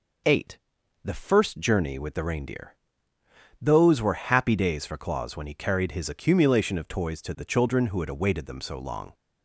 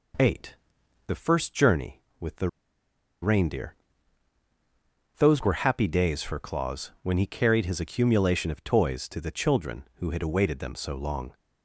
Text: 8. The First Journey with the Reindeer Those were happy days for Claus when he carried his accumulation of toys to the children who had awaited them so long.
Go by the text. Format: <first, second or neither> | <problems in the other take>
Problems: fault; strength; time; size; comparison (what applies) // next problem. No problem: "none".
first | pauses between "the" and "Reindeer"; noticeable; at 2.4 s; 0.74 s long // pauses between "Reindeer" and "Those"; strong; at 3.7 s; 1.4 s long; noticeable in the first